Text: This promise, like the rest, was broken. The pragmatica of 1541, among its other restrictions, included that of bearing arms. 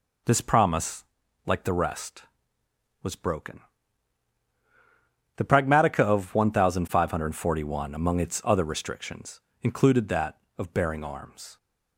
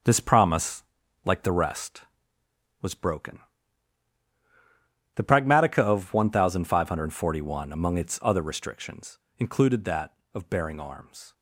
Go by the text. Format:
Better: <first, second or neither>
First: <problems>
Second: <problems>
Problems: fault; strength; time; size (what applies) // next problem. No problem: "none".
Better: first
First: none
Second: gets quieter; throughout; 6.5 dB